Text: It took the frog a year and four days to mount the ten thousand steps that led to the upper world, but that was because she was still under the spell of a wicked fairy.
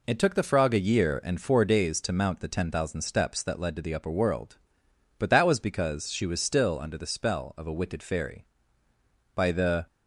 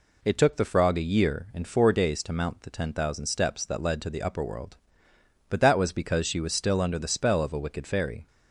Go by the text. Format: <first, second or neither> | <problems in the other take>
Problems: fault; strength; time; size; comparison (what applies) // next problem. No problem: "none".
second | goes on to say "By the"; from 9.3 s on; 0.50 s long